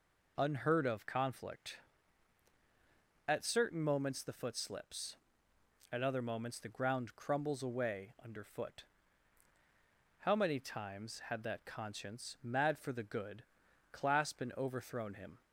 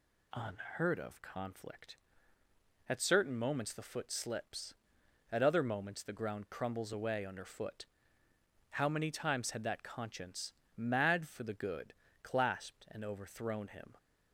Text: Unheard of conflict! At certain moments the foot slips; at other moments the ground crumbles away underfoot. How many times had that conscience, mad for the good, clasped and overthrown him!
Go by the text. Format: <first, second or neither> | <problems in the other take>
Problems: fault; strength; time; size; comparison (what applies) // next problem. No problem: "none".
neither | none